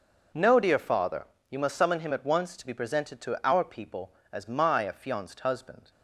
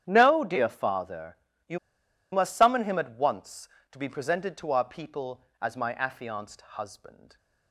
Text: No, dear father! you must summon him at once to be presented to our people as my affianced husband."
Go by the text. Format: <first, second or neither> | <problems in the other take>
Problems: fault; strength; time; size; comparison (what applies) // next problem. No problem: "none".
first | starts louder than the rest; strong; until 1.0 s; 10 dB // pauses between "you" and "must"; noticeable; at 1.7 s; 0.53 s long